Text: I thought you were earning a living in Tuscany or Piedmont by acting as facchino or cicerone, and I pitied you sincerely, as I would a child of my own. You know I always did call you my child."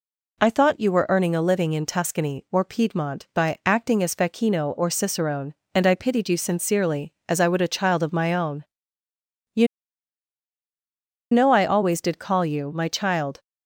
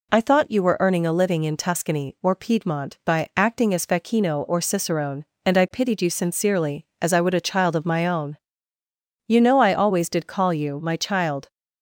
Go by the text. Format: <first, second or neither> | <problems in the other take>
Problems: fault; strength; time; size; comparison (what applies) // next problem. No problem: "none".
second | pauses between "You" and "know"; strong; at 9.6 s; 1.6 s long